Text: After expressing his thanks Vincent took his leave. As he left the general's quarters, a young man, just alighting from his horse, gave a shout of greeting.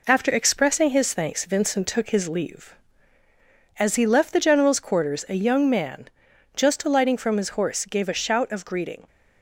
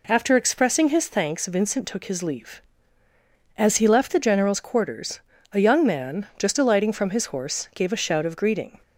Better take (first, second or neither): second